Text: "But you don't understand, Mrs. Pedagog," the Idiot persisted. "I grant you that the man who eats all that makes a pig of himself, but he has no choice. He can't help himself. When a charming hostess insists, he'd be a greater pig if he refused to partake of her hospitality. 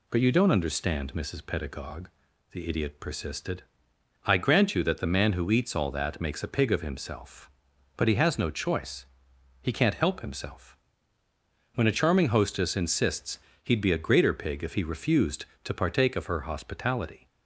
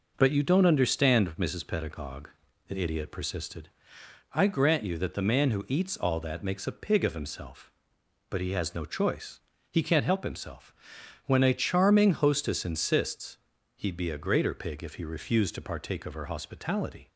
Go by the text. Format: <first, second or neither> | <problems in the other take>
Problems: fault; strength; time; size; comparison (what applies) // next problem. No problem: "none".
neither | none